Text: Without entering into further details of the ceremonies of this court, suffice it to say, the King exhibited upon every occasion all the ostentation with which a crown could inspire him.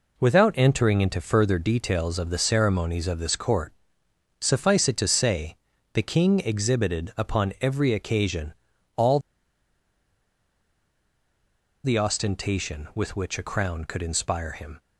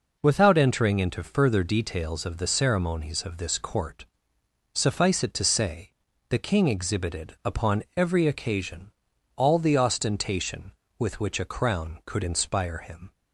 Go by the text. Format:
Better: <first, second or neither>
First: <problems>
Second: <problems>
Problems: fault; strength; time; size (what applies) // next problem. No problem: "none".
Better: second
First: pauses between "occasion" and "all"; at 8.5 s; 0.42 s long // pauses between "all" and "the"; strong; at 9.1 s; 2.6 s long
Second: pauses between "occasion" and "all"; noticeable; at 8.9 s; 0.46 s long